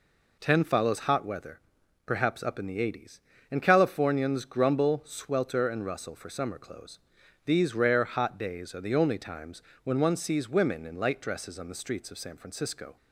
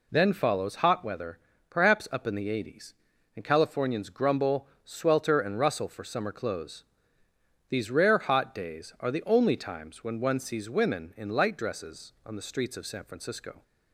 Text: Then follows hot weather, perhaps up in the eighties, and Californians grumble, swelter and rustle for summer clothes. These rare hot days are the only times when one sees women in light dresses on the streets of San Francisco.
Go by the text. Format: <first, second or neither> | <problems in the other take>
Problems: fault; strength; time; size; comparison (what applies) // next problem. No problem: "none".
second | says "Ten" for "Then"; at 0.3 s // pauses between "times" and "when"; slight; at 9.6 s; 0.22 s long